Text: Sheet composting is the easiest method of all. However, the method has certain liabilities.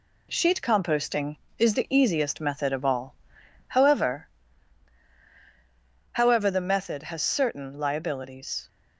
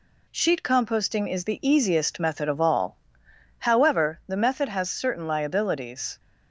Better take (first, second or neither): second